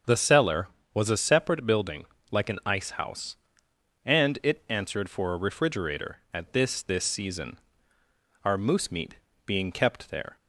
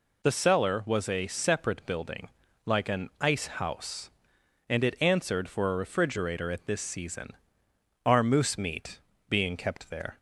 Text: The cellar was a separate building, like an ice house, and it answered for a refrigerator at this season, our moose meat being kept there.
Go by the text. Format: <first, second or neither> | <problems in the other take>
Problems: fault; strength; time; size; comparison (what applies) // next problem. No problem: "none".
second | starts louder than the rest; until 1.3 s; 7 dB // says "this" twice; at 6.8 s // pauses between "meat" and "being"; slight; at 9.1 s; 0.28 s long; slight in the second